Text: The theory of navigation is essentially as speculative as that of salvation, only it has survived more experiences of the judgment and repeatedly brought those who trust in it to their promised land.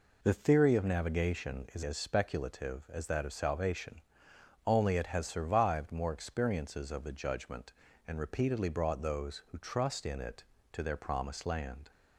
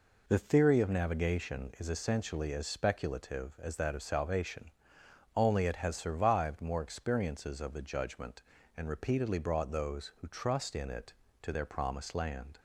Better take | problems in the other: second | skips "essentially"; at 1.8 s

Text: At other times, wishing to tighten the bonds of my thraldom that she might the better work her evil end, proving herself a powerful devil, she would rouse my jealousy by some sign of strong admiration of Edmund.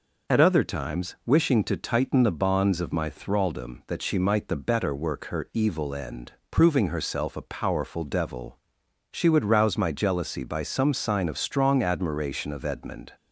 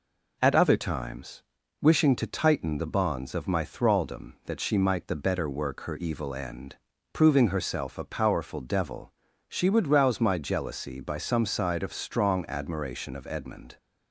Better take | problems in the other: first | says "side" for "sign"; at 11.4 s

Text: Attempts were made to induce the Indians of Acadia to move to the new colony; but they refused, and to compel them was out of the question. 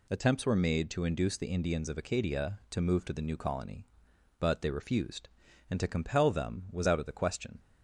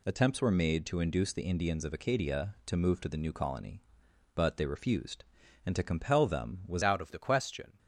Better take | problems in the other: first | changes voice at "out"; from 6.8 s on; 0.9 s long

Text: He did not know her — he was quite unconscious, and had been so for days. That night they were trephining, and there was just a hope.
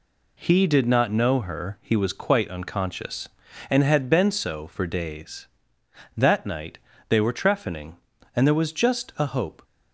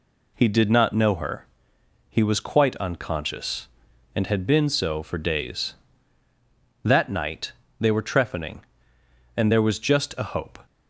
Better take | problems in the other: neither | pauses between "night" and "they"; slight; the same in both

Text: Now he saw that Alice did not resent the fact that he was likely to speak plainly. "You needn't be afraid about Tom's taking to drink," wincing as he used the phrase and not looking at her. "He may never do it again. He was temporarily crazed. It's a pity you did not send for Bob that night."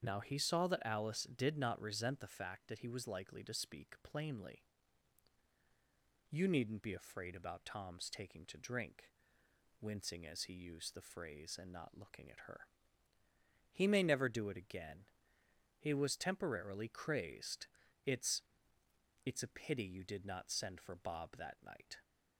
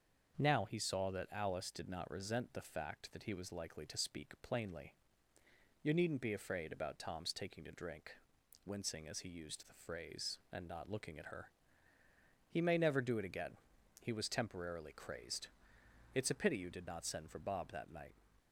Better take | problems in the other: second | starts louder than the rest; strong; until 1.0 s; 7.5 dB; also in the second // says "It's" twice; at 19.2 s

